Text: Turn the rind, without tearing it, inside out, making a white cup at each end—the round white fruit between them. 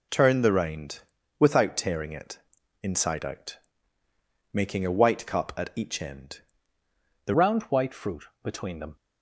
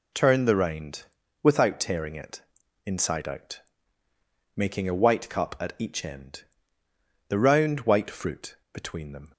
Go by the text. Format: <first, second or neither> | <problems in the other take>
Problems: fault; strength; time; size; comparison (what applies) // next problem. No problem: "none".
second | changes voice at "round"; from 7.3 s on; 1.6 s long // pauses between "fruit" and "between"; slight; at 8.2 s; 0.16 s long; slight in the second